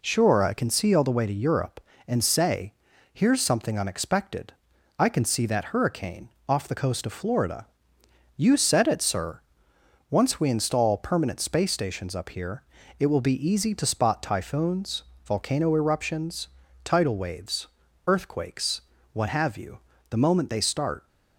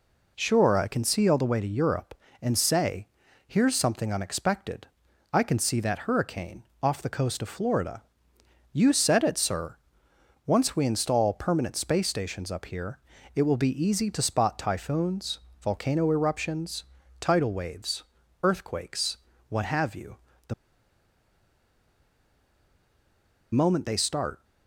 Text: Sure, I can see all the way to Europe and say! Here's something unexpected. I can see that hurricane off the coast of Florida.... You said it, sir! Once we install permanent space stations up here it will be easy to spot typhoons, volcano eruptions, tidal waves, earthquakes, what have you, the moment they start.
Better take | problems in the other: first | pauses between "hurricane" and "off"; slight; at 6.6 s; 0.20 s long; slight in the first // pauses between "here" and "it"; slight; at 12.9 s; 0.36 s long; slight in the first // pauses between "the" and "moment"; strong; at 20.5 s; 2.9 s long

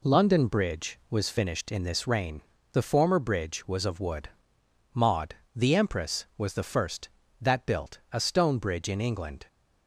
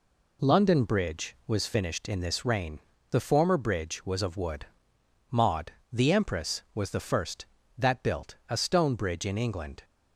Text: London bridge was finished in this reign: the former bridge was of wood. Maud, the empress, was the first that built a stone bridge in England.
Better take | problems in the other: neither | none

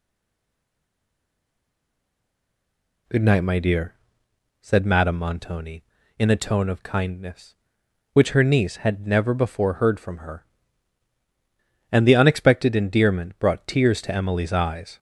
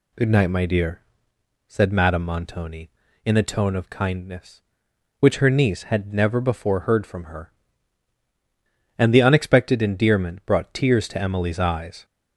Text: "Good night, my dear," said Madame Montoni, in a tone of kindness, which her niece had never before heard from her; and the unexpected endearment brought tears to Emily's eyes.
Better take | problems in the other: second | stays silent before the first word; strong; until 3.0 s; 3.0 s long

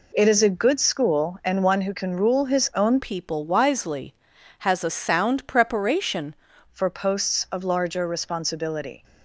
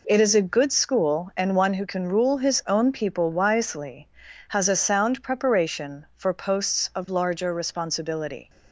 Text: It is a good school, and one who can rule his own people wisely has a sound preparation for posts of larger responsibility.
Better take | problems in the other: second | changes voice from "people" to "preparation"; from 2.9 to 6.3 s; 3.4 s long

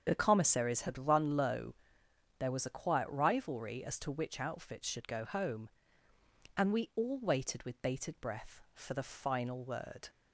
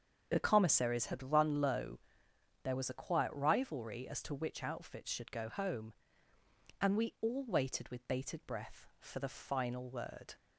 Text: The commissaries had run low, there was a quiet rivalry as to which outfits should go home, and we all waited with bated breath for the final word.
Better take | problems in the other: neither | starts louder than the rest; the same in both

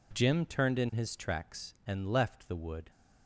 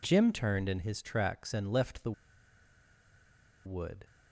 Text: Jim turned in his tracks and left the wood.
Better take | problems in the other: first | pauses between "the" and "wood"; strong; at 2.1 s; 1.5 s long

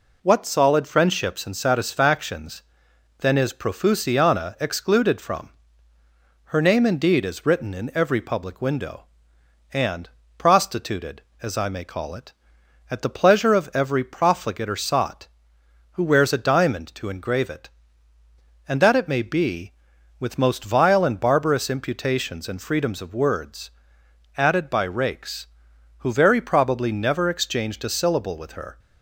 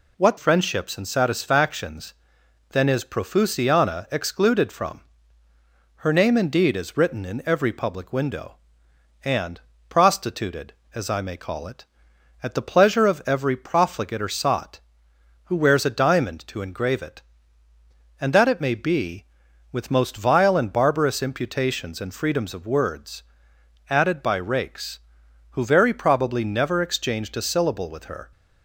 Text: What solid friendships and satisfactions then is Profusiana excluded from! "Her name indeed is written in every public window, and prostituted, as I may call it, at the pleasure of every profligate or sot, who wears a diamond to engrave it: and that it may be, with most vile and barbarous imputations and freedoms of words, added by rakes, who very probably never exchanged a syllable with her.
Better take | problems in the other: first | skips "solid"; at 0.3 s // pauses between "satisfactions" and "then"; noticeable; at 2.1 s; 0.58 s long; noticeable in the first // pauses between "and" and "prostituted"; slight; at 9.6 s; 0.26 s long; slight in the first

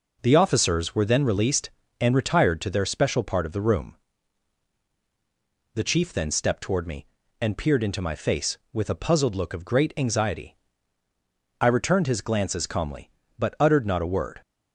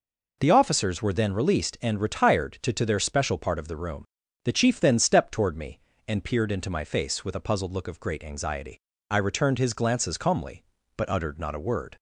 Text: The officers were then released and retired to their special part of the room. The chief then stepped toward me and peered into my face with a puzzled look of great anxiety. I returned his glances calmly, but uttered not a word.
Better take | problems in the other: first | says "to" twice; at 2.7 s

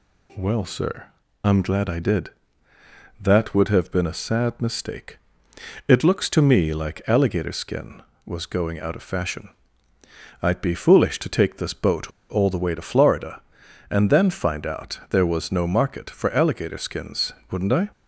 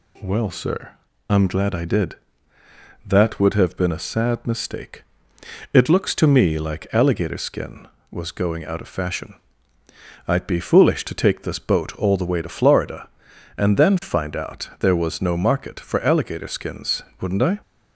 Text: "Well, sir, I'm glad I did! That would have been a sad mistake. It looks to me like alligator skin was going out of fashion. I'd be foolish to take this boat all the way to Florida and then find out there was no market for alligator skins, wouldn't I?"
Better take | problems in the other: second | pauses between "boat" and "all"; slight; at 12.0 s; 0.20 s long

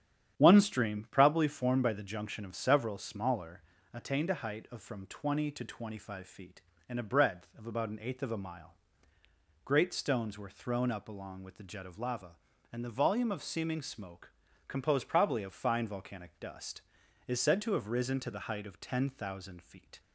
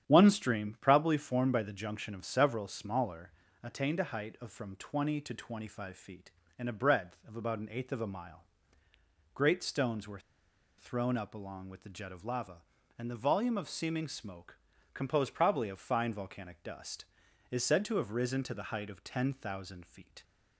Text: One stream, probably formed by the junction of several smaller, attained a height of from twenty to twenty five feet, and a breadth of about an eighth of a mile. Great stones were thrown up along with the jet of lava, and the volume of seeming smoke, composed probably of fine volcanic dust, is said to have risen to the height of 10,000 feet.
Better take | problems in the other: first | starts louder than the rest; strong; until 1.1 s; 9.5 dB; strong in the first // pauses between "were" and "thrown"; noticeable; at 10.1 s; 0.59 s long

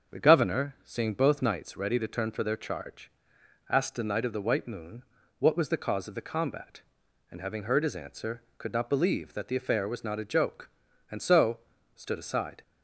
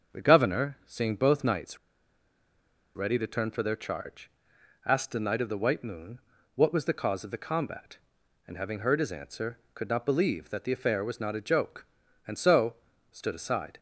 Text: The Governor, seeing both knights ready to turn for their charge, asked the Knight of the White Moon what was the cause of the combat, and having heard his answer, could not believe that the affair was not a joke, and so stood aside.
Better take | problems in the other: first | starts louder than the rest; until 1.2 s; 7 dB; also in the first // pauses between "knights" and "ready"; at 1.7 s; 1.1 s long // pauses between "Moon" and "what"; slight; at 6.2 s; 0.34 s long; slight in the first // pauses between "so" and "stood"; slight; at 12.7 s; 0.36 s long; slight in the first

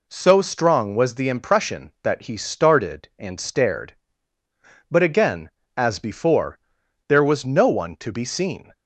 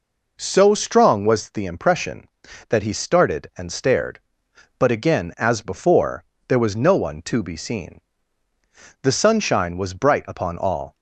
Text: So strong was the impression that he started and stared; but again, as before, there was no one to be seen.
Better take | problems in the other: first | goes on to say "The sunshine was bright upon all"; strong; from 9.0 s on; 1.9 s long

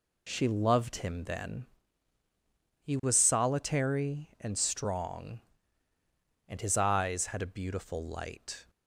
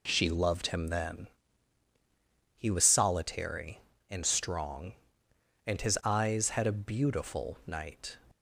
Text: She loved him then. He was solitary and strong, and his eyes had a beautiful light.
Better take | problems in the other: first | says "night" for "light"; at 7.6 s

